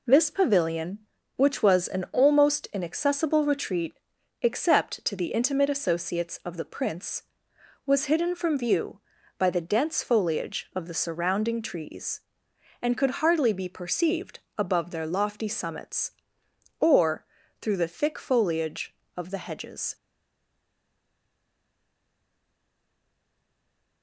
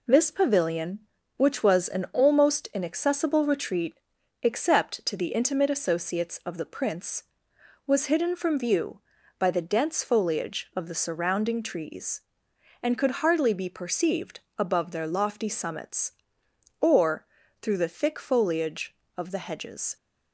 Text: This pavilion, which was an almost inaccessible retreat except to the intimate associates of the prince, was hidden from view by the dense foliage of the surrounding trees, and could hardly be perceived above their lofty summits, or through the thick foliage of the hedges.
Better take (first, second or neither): second